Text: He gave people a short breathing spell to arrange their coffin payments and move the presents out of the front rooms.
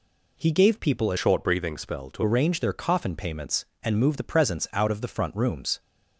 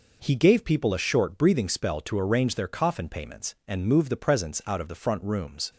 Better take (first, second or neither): second